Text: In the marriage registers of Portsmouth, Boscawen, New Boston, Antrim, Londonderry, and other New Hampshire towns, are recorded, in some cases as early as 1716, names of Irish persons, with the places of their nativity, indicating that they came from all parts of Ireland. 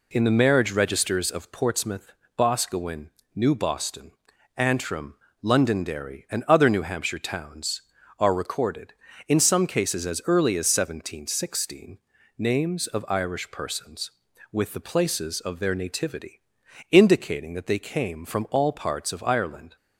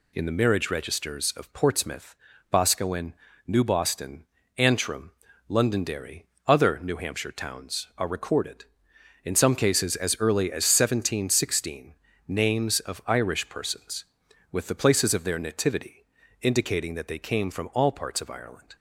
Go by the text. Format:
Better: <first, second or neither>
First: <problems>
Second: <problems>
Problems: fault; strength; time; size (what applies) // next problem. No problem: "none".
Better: first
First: none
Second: skips "and"; at 6.3 s